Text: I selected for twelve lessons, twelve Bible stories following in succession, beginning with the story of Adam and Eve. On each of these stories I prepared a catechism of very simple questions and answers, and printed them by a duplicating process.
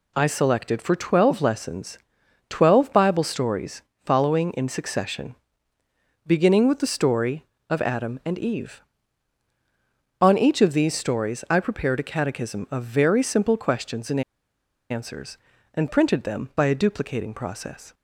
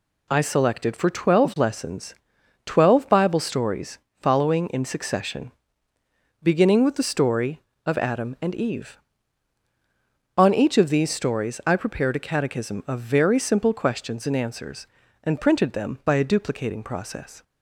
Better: second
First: pauses between "stories" and "following"; slight; at 3.8 s; 0.22 s long // pauses between "and" and "answers"; noticeable; at 14.2 s; 0.69 s long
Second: pauses between "stories" and "following"; slight; at 3.9 s; 0.22 s long

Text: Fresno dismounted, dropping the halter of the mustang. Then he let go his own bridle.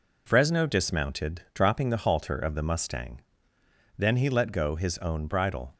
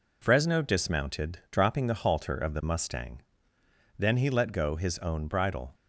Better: neither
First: none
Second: none

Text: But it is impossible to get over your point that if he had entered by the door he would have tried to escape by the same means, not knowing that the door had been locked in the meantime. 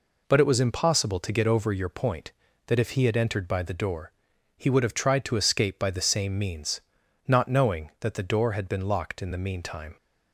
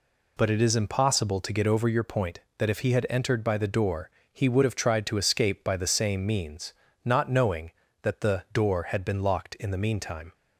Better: second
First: says "was" for "is"; at 0.4 s // pauses between "door" and "he"; noticeable; at 4.1 s; 0.46 s long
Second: pauses between "door" and "he"; slight; at 4.0 s; 0.22 s long

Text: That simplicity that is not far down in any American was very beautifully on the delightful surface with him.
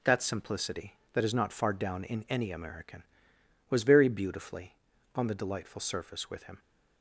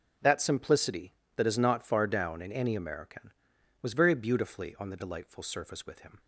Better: neither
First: none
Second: none

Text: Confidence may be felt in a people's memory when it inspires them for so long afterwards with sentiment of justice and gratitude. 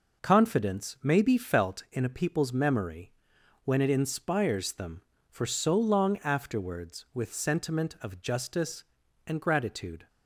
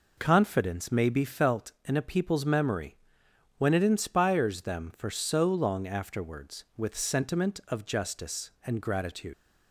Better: first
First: pauses between "memory" and "when"; noticeable; at 3.1 s; 0.50 s long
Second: pauses between "memory" and "when"; noticeable; at 2.9 s; 0.60 s long // leaves "gratitude" unfinished; at 9.3 s; 110 ms

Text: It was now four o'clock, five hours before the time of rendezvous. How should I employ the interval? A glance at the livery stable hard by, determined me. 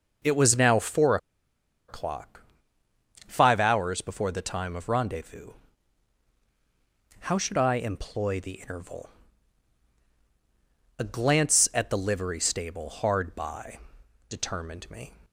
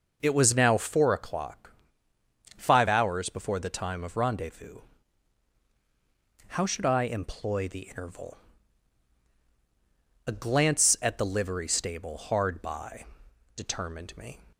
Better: second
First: pauses between "four" and "o'clock"; noticeable; at 1.1 s; 0.71 s long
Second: none

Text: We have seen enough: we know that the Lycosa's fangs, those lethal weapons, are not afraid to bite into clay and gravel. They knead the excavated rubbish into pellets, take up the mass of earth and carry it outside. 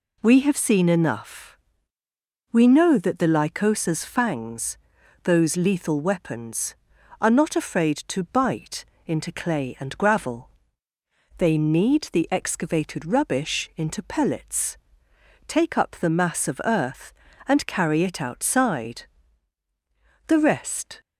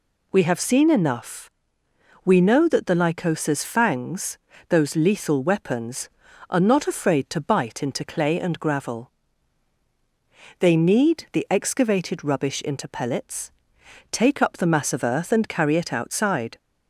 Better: second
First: pauses between "bite" and "into"; slight; at 8.8 s; 0.22 s long // goes on to say "The rest"; noticeable; from 20.2 s on; 0.74 s long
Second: none

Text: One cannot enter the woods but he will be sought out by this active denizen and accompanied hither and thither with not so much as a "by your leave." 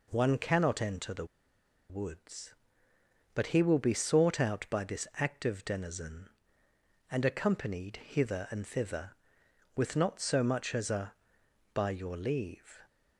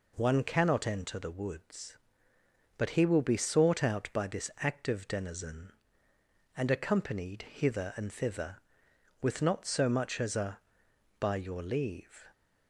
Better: second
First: pauses between "the" and "woods"; noticeable; at 1.2 s; 0.64 s long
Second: none

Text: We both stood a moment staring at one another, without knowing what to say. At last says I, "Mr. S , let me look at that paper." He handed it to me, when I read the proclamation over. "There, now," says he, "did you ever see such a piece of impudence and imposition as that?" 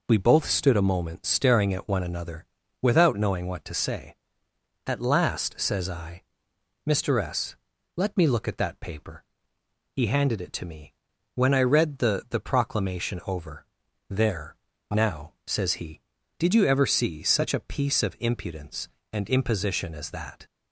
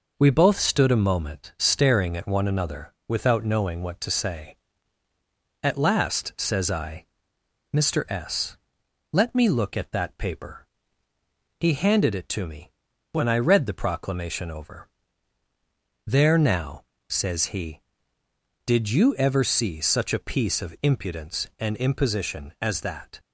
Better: second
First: says "the" twice; at 12.2 s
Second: none

